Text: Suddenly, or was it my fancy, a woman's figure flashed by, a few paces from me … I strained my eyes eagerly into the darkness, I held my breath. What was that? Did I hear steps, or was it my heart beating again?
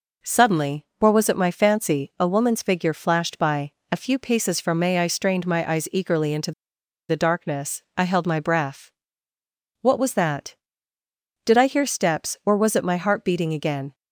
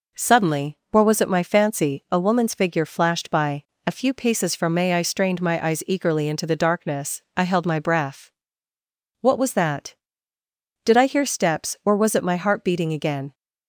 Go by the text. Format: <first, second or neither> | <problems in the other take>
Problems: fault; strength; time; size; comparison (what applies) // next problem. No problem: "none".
second | pauses between "into" and "the"; noticeable; at 6.5 s; 0.58 s long